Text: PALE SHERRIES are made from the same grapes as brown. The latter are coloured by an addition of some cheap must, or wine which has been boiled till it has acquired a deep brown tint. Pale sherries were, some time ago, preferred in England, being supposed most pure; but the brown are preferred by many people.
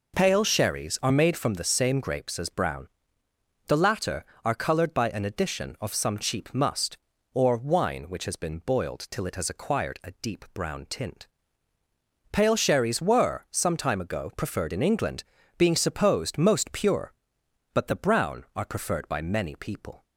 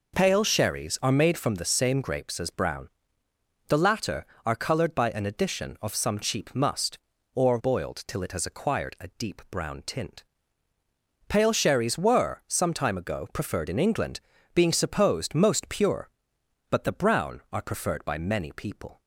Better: first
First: none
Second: skips "wine which has been"; at 7.5 s

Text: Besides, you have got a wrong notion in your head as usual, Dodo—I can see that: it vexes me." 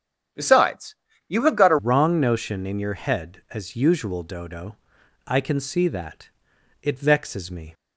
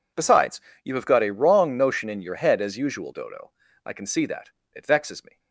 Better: second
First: starts louder than the rest; strong; until 1.6 s; 8.5 dB // changes voice at "wrong"; from 1.7 s on; 6.0 s long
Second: none

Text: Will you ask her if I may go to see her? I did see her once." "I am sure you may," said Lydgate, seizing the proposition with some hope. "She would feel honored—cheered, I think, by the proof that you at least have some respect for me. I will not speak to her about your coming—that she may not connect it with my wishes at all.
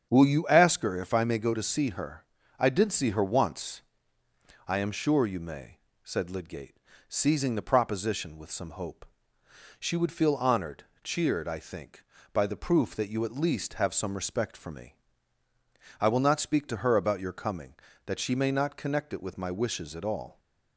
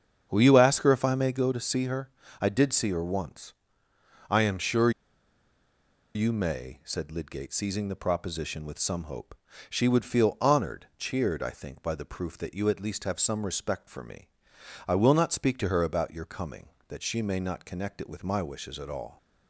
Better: first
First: starts louder than the rest; strong; until 1.1 s; 7.5 dB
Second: starts louder than the rest; strong; until 1.3 s; 7 dB // pauses between "sure" and "you"; at 4.9 s; 1.2 s long

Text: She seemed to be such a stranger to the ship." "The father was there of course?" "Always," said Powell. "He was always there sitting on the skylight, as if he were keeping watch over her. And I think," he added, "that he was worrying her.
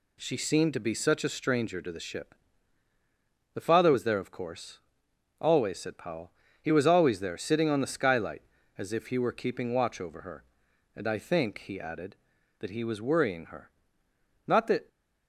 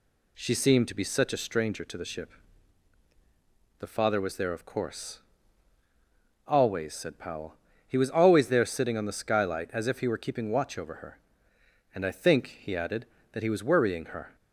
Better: second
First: goes on to say "Not that"; slight; from 14.4 s on; 0.40 s long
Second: none

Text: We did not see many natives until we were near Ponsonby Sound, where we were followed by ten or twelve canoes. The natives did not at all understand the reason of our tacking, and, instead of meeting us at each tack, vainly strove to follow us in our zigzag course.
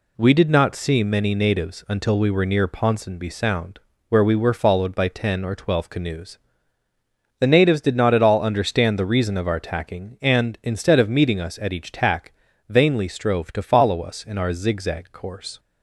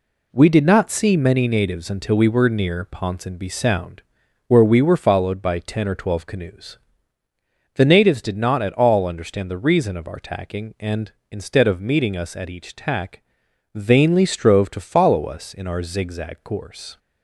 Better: neither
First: none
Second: none

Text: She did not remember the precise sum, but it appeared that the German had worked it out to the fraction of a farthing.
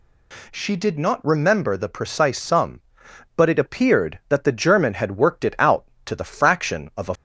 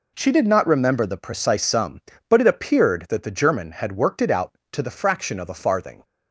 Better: second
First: stops before "farthing"; at 7.1 s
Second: none

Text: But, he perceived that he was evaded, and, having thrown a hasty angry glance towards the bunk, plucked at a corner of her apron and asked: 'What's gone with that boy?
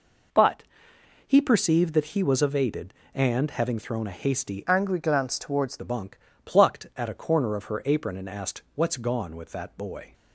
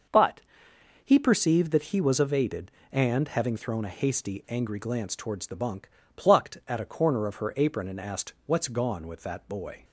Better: second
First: changes voice from "angry" to "towards"; from 4.6 to 5.7 s; 1.1 s long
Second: none

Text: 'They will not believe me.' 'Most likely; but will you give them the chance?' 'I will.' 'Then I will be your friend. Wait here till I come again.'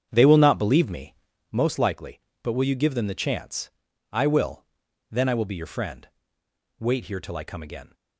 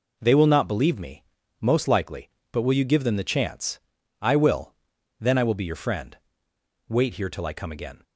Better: second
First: starts louder than the rest; strong; until 1.5 s; 8 dB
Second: none

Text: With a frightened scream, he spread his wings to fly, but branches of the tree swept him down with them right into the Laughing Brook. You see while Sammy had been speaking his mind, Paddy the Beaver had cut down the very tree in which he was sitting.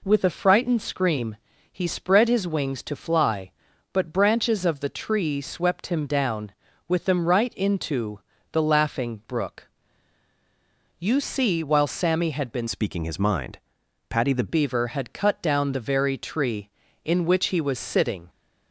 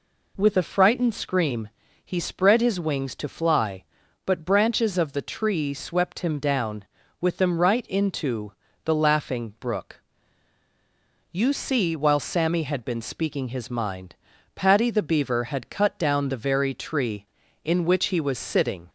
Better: second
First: pauses between "into" and "the"; slight; at 8.1 s; 0.32 s long // changes voice from "speaking" to "the"; from 12.6 to 14.4 s; 1.8 s long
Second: pauses between "into" and "the"; slight; at 8.5 s; 0.32 s long

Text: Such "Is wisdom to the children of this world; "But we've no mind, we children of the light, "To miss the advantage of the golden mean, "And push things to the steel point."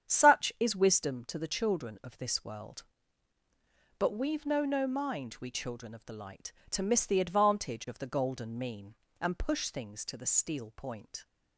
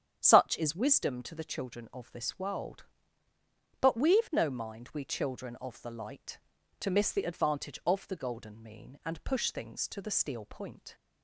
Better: second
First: starts louder than the rest; strong; until 1.1 s; 8.5 dB // says "no" twice; at 4.6 s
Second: starts louder than the rest; strong; until 1.2 s; 9 dB

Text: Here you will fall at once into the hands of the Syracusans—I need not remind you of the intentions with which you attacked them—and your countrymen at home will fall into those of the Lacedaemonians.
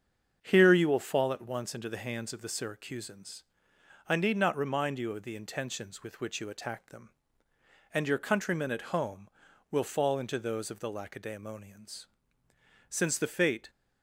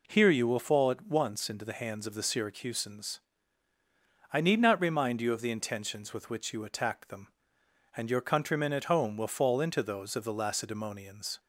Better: second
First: starts louder than the rest; until 1.4 s; 7 dB // goes on to say "Since the fate"; noticeable; from 12.8 s on; 0.82 s long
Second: none

